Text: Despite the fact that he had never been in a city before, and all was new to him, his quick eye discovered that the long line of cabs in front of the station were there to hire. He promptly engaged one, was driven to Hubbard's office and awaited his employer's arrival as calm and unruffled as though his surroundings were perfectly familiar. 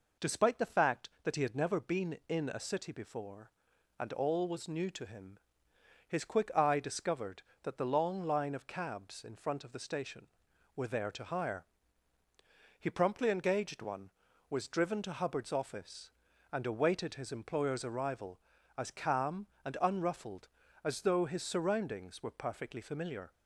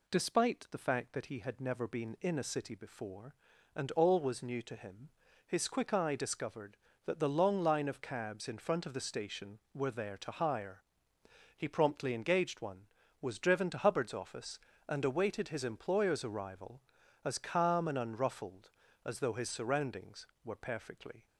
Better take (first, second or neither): first